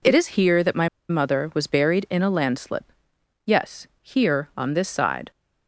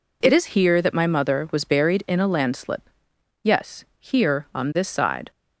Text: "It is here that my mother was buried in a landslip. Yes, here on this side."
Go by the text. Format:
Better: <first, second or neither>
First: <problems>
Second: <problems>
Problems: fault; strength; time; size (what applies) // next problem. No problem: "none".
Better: second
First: pauses between "my" and "mother"; slight; at 0.8 s; 0.21 s long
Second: none